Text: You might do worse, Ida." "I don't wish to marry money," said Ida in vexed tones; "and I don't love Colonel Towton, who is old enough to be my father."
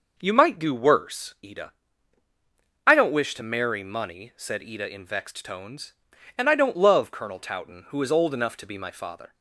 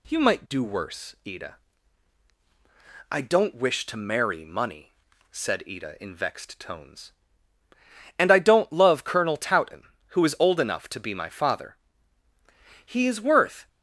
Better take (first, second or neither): first